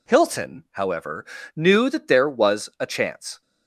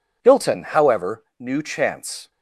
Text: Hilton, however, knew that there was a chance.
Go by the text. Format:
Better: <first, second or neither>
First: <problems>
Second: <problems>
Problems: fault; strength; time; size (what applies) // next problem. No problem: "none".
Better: first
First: none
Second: skips "that there was a"; at 1.6 s